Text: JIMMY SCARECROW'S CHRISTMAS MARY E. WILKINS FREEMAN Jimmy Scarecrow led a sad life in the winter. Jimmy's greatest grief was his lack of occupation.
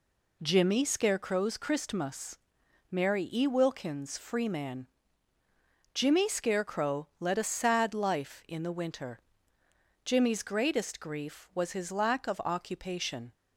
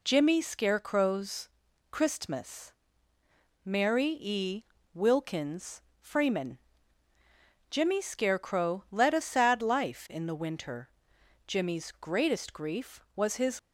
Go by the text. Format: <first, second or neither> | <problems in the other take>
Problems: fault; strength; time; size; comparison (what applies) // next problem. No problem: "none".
first | pauses between "SCARECROW'S" and "CHRISTMAS"; at 1.4 s; 0.44 s long // pauses between "CHRISTMAS" and "MARY"; noticeable; at 2.7 s; 0.92 s long; noticeable in the first // pauses between "WILKINS" and "FREEMAN"; slight; at 5.7 s; 0.20 s long // pauses between "FREEMAN" and "Jimmy"; at 6.5 s; 1.1 s long; also in the first // stops before "lack of occupation"; at 13.5 s